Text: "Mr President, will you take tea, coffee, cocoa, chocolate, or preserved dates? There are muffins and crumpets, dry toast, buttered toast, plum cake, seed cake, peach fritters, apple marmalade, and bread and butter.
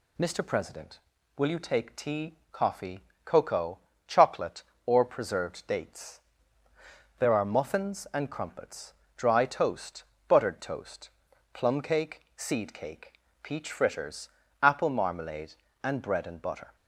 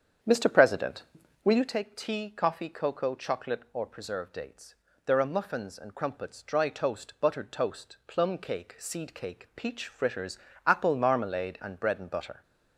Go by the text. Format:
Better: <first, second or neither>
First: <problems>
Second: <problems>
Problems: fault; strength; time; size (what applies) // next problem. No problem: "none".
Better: first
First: none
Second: starts louder than the rest; strong; until 1.8 s; 8 dB